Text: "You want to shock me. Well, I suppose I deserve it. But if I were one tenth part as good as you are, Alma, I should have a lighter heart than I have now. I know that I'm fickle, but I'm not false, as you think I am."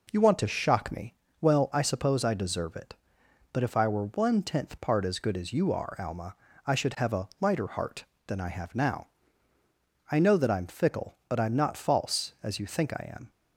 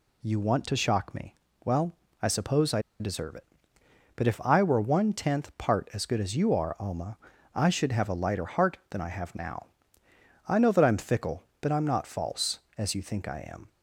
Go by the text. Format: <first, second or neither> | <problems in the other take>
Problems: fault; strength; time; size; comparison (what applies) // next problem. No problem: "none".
first | pauses between "I" and "deserve"; slight; at 2.8 s; 0.19 s long